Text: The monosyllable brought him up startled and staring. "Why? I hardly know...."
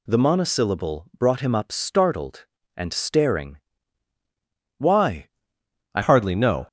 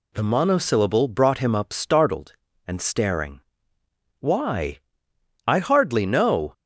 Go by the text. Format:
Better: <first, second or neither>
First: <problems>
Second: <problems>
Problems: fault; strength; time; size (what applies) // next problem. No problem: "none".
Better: second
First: changes voice at "hardly"; from 6.0 s on; 0.6 s long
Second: none